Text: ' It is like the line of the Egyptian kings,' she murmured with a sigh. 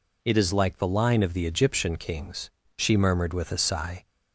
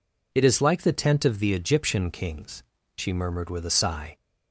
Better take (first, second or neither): first